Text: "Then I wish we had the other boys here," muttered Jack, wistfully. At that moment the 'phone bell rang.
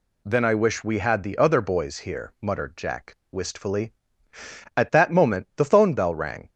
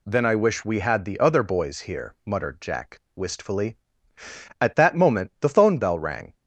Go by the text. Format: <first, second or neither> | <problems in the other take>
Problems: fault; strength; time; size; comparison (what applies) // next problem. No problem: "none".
neither | none